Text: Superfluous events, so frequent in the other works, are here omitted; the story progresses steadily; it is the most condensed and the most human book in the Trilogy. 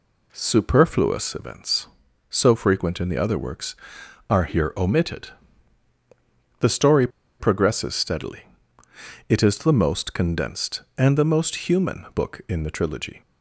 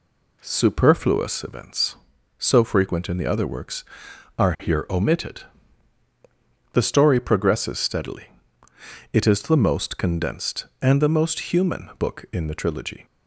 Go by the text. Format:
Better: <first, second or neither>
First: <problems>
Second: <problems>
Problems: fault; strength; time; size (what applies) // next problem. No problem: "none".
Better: second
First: pauses between "story" and "progresses"; slight; at 7.0 s; 0.31 s long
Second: none